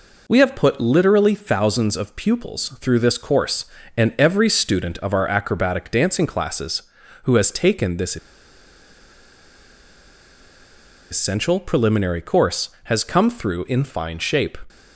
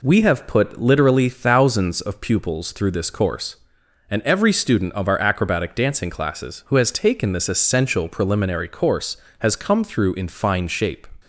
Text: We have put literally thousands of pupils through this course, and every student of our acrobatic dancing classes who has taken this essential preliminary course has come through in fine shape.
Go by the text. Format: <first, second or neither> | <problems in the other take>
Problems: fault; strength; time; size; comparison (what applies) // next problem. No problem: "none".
second | pauses between "this" and "essential"; strong; at 8.1 s; 2.9 s long